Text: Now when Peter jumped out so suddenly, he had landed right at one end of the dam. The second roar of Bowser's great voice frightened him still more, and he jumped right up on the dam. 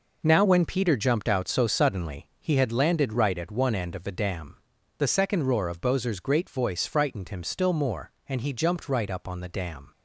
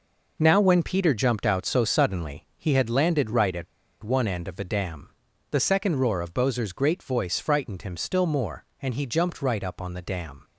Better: first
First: none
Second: pauses between "at" and "one"; at 3.6 s; 0.38 s long

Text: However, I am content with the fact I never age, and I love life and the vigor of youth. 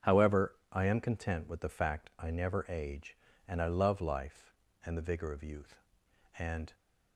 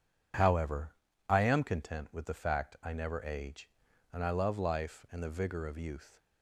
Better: second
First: starts louder than the rest; strong; until 1.1 s; 7.5 dB // goes on to say "And"; slight; from 6.3 s on; 0.32 s long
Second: none

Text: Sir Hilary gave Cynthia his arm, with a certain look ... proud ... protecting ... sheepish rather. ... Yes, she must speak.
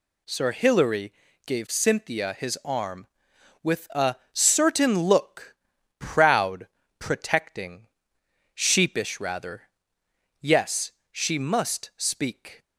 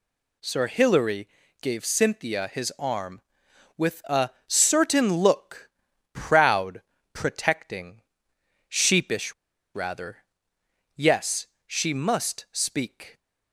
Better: first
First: pauses between "Hilary" and "gave"; slight; at 1.1 s; 0.34 s long // pauses between "a" and "certain"; slight; at 4.1 s; 0.16 s long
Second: pauses between "Hilary" and "gave"; slight; at 1.2 s; 0.34 s long // pauses between "a" and "certain"; slight; at 4.2 s; 0.16 s long // pauses between "sheepish" and "rather"; at 9.3 s; 0.40 s long

